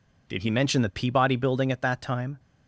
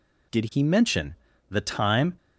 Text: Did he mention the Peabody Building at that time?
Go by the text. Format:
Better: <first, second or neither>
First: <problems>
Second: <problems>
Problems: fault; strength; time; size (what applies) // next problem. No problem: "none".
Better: first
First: none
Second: pauses between "mention" and "the"; slight; at 1.1 s; 0.34 s long // skips "Peabody Building at that"; at 1.6 s